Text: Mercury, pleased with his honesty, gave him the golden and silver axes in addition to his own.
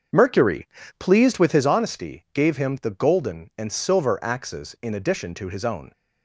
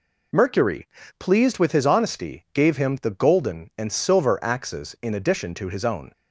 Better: second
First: starts louder than the rest; until 1.7 s; 7 dB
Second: none

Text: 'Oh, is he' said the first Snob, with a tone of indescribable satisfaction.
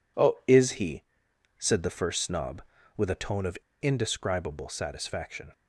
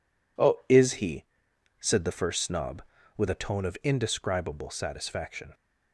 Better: second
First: pauses between "he" and "said"; noticeable; at 1.0 s; 0.52 s long // pauses between "of" and "indescribable"; slight; at 3.5 s; 0.24 s long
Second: pauses between "he" and "said"; noticeable; at 1.2 s; 0.52 s long

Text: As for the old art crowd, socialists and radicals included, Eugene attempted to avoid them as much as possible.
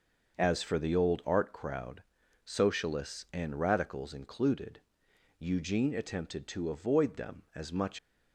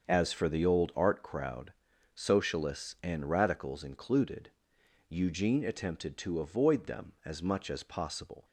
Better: second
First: starts louder than the rest; until 1.3 s; 6 dB // stops before "as possible"; at 7.9 s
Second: starts louder than the rest; until 1.0 s; 6.5 dB

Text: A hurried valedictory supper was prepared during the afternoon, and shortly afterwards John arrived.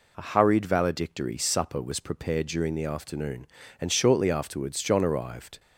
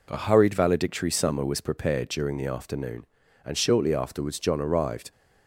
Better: first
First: none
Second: says "summer" for "supper"; at 1.1 s

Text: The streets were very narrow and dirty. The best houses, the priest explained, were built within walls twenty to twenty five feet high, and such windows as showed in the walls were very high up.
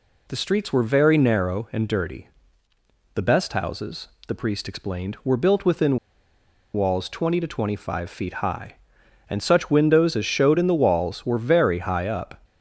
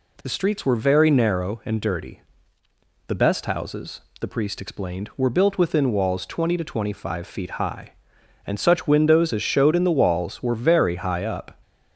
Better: second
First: pauses between "within" and "walls"; noticeable; at 5.9 s; 0.76 s long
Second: none

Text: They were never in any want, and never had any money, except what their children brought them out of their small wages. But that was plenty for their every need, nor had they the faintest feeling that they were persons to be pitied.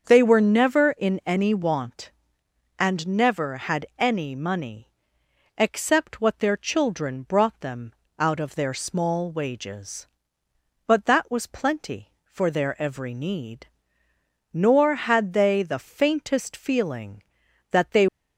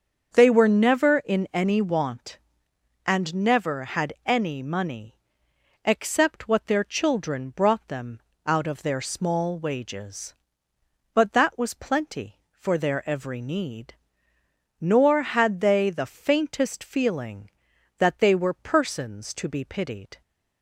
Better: second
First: starts louder than the rest; until 1.0 s; 6.5 dB // pauses between "them" and "out"; slight; at 7.9 s; 0.24 s long // stops before "were persons to be pitied"; at 18.0 s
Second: starts louder than the rest; until 1.3 s; 6.5 dB // pauses between "them" and "out"; slight; at 8.2 s; 0.24 s long

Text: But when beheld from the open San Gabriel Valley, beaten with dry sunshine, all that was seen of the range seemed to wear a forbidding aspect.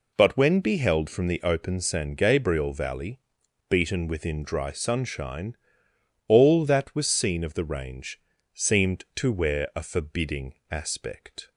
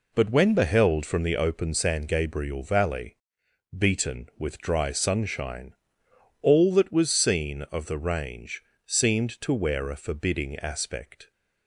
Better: second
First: says "within" for "with"; at 4.0 s // pauses between "range" and "seemed"; slight; at 8.1 s; 0.34 s long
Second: pauses between "range" and "seemed"; slight; at 8.6 s; 0.24 s long

